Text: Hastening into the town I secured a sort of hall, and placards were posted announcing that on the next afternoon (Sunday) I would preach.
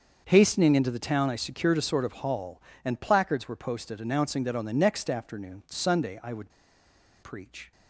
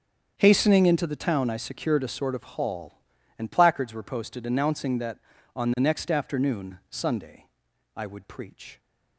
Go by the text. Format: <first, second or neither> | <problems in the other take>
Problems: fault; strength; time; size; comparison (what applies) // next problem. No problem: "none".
second | starts louder than the rest; until 1.2 s; 6.5 dB; strong in the second // pauses between "would" and "preach"; noticeable; at 6.5 s; 0.72 s long